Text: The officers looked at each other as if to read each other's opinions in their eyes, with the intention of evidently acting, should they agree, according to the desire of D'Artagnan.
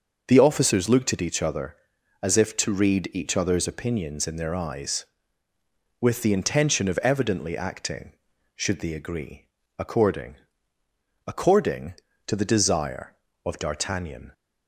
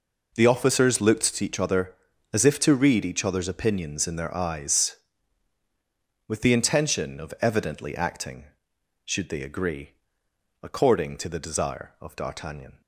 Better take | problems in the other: second | starts louder than the rest; until 1.2 s; 6.5 dB // says "according" twice; at 11.2 s

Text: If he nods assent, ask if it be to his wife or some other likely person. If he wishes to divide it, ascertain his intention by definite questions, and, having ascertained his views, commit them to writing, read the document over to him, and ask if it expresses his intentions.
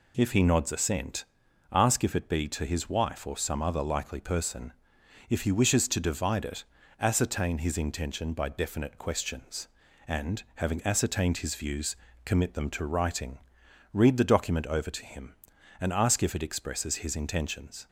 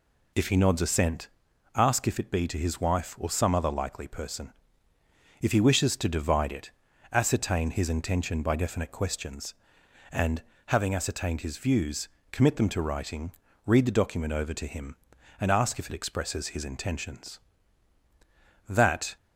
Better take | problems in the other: first | goes on to say "That"; slight; from 18.6 s on; 0.48 s long

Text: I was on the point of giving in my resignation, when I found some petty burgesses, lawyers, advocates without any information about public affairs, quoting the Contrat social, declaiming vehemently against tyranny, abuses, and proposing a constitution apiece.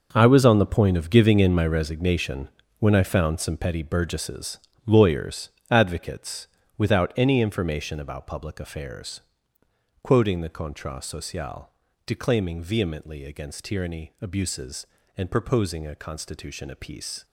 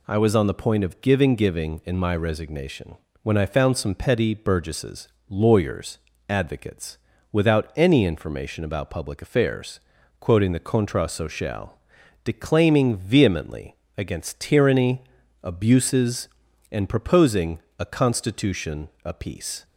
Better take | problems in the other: first | says "giving" twice; at 1.3 s // pauses between "advocates" and "without"; slight; at 6.9 s; 0.34 s long; slight in the first // pauses between "vehemently" and "against"; slight; at 13.7 s; 0.20 s long // pauses between "proposing" and "a"; slight; at 17.6 s; 0.18 s long // pauses between "constitution" and "apiece"; slight; at 18.8 s; 0.16 s long

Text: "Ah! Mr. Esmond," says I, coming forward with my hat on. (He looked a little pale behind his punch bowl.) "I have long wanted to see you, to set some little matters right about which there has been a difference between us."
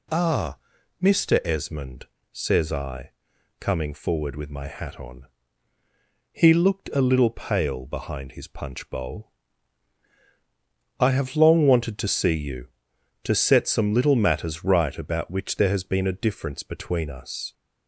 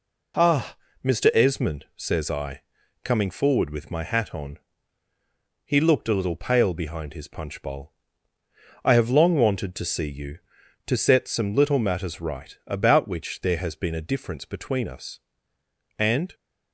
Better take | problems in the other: first | goes on to say "And"; slight; from 15.9 s on; 0.36 s long

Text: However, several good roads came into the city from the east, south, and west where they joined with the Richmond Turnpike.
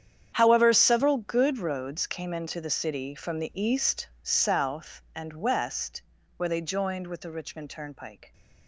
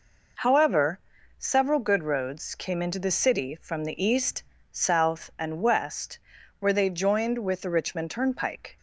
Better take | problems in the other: second | gets quieter; strong; throughout; 15.5 dB // pauses between "west" and "where"; at 6.0 s; 0.38 s long; also in the second

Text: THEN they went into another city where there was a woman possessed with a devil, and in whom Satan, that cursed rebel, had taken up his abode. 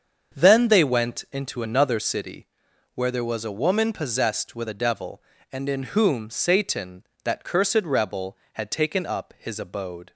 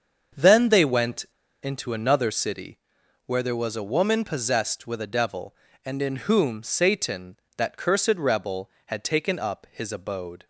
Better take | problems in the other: first | starts louder than the rest; until 1.7 s; 7 dB; also in the first // pauses between "went" and "into"; at 1.2 s; 0.36 s long // pauses between "city" and "where"; noticeable; at 2.7 s; 0.48 s long; noticeable in the first

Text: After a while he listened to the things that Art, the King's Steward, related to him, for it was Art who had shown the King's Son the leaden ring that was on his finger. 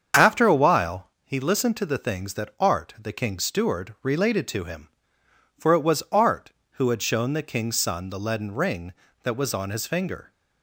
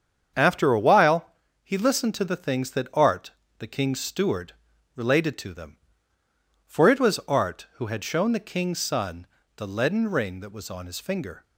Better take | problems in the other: first | starts louder than the rest; strong; until 1.7 s; 7.5 dB; strong in the first // pauses between "while" and "he"; slight; at 1.2 s; 0.34 s long // says "them" for "him"; at 5.5 s // pauses between "Son" and "the"; slight; at 9.2 s; 0.30 s long

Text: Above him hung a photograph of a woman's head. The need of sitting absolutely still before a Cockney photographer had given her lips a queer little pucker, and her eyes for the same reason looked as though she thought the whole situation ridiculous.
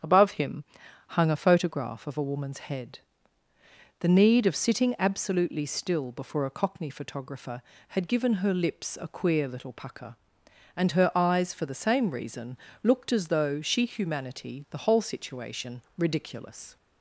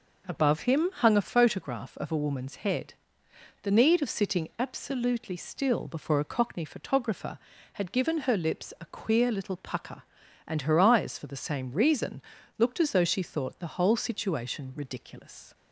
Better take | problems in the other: second | starts louder than the rest; strong; until 1.4 s; 8 dB // pauses between "him" and "hung"; at 0.6 s; 0.44 s long // pauses between "reason" and "looked"; slight; at 12.5 s; 0.26 s long; slight in the second // says "humanity" for "thought"; at 13.8 s // pauses between "situation" and "ridiculous"; slight; at 15.8 s; 0.16 s long

